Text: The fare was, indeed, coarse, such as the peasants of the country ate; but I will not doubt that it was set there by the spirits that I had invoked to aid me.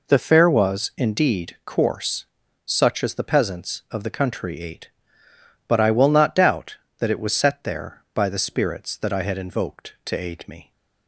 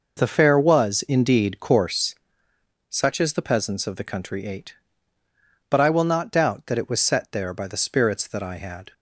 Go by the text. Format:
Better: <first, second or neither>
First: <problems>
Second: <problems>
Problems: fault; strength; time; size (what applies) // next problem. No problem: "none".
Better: first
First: none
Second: stops before "invoked to aid me"; at 8.9 s